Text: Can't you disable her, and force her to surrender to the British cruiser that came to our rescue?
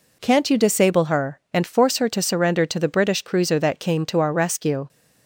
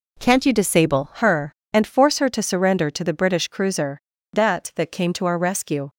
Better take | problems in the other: first | says "that" twice; at 4.7 s

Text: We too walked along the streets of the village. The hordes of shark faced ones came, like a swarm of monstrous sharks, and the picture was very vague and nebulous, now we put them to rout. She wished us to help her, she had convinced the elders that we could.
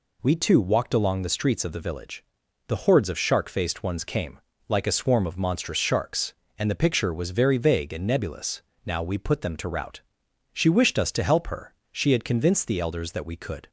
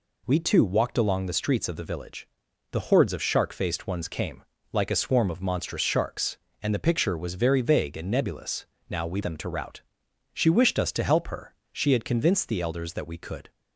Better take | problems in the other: first | skips "put"; at 9.2 s

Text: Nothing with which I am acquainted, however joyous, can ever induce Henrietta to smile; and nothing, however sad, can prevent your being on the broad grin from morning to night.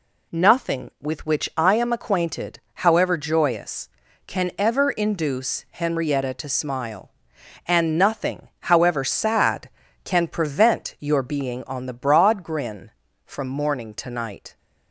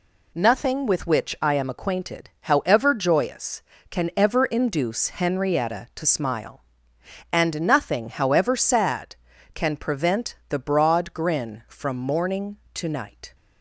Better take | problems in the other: first | skips "your being on"; at 10.4 s

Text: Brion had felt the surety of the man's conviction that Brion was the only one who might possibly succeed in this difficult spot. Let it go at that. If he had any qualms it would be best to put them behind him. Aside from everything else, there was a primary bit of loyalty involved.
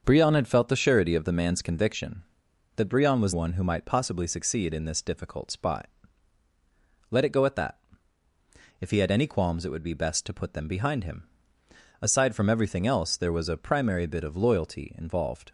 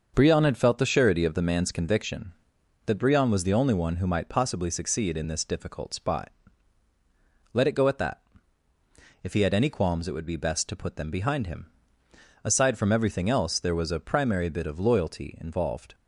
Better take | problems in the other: second | starts louder than the rest; until 1.0 s; 6.5 dB; also in the second // skips "the only"; at 3.3 s

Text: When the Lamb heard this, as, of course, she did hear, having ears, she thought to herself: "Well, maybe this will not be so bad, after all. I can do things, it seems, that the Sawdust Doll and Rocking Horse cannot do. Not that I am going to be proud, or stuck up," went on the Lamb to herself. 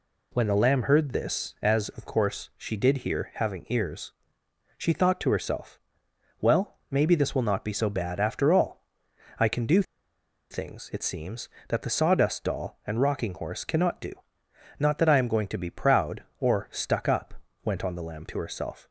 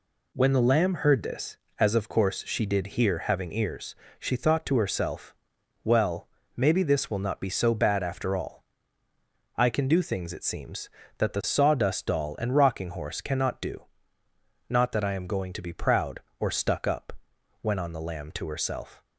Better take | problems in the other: second | pauses between "do" and "things"; noticeable; at 9.8 s; 0.68 s long

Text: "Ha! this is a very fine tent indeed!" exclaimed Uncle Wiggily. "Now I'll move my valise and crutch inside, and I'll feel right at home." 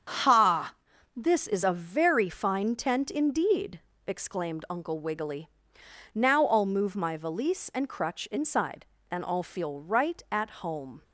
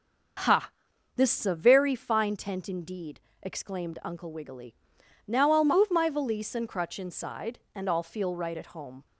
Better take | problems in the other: neither | starts louder than the rest; the same in both

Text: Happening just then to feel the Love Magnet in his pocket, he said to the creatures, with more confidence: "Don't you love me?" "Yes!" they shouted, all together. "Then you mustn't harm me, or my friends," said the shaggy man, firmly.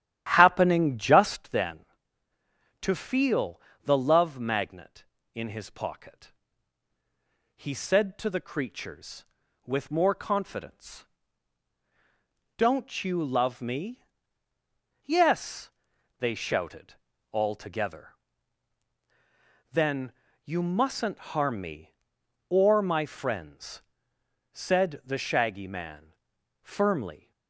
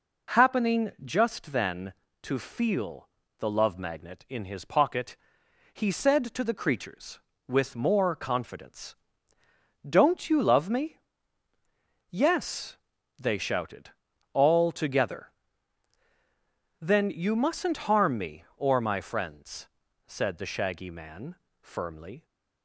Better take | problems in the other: second | starts louder than the rest; strong; until 1.6 s; 11.5 dB // pauses between "feel" and "the"; slight; at 3.6 s; 0.24 s long; slight in the second // pauses between "Then" and "you"; slight; at 20.1 s; 0.32 s long

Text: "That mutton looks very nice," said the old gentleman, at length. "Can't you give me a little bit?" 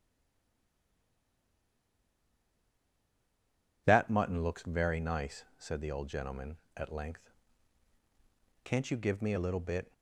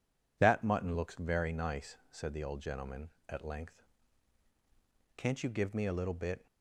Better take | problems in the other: second | stays silent before the first word; strong; until 3.8 s; 3.8 s long

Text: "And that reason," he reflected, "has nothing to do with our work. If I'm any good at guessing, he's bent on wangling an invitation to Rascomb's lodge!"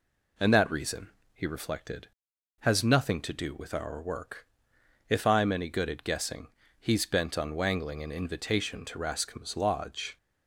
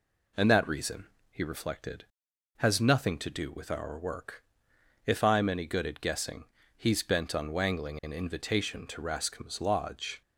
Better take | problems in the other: neither | none

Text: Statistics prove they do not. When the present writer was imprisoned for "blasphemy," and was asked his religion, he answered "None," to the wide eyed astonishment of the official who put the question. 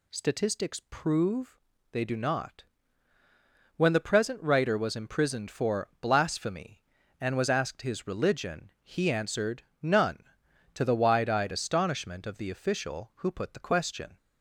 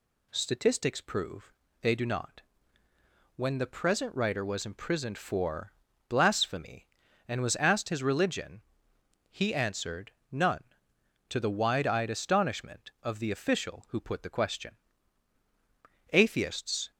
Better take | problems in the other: first | pauses between "prove" and "they"; slight; at 1.5 s; 0.28 s long; slight in the first // pauses between "for" and "blasphemy"; slight; at 5.7 s; 0.36 s long // pauses between "answered" and "None"; slight; at 10.1 s; 0.20 s long; slight in the first // goes on to say "Atheists"; noticeable; from 16.1 s on; 0.78 s long

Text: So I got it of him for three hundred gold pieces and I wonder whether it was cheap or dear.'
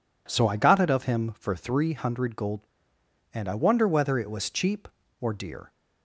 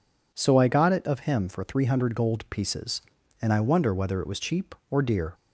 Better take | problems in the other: second | skips "pieces"; at 2.9 s

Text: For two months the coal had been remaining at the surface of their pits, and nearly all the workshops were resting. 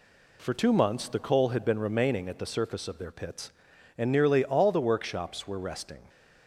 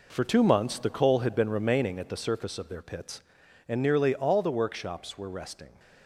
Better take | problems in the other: first | gets quieter; strong; throughout; 9.5 dB

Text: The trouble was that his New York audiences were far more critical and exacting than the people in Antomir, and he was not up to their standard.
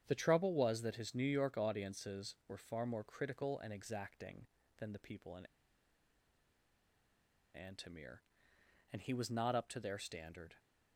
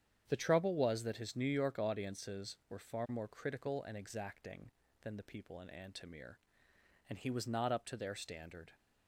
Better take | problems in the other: second | starts louder than the rest; strong; until 1.0 s; 8.5 dB; strong in the second // pauses between "in" and "Antomir"; strong; at 5.4 s; 2.0 s long

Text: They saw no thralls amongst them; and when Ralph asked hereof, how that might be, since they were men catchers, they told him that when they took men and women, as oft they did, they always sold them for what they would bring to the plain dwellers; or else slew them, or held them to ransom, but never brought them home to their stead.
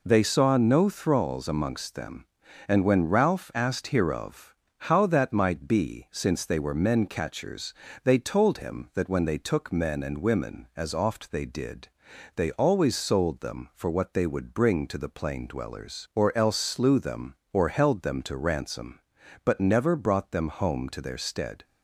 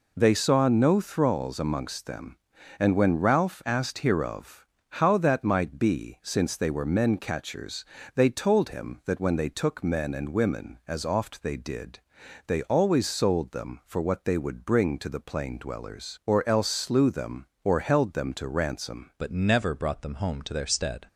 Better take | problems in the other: first | changes voice at "but"; from 19.1 s on; 1.9 s long

